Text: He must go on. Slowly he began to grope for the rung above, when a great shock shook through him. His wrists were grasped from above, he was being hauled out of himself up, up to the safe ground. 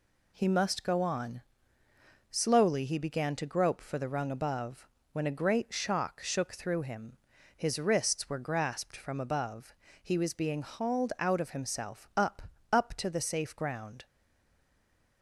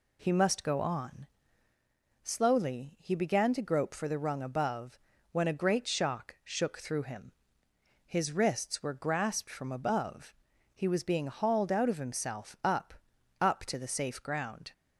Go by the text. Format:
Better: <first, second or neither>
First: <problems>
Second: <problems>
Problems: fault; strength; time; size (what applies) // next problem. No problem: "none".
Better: second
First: stays silent after the last word; noticeable; from 14.0 s on; 1.2 s long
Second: none